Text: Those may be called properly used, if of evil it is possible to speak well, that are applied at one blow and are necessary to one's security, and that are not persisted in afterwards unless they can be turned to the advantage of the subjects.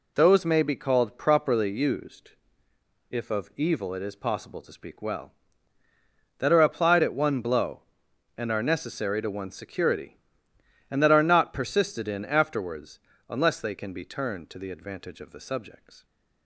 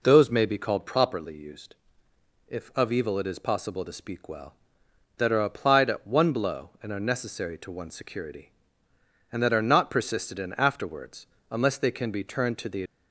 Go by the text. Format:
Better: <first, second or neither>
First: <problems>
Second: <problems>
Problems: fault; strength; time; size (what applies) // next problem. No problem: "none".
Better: first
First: pauses between "afterwards" and "unless"; slight; at 12.9 s; 0.30 s long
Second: pauses between "afterwards" and "unless"; slight; at 11.2 s; 0.24 s long // stops before "advantage of the subjects"; at 12.8 s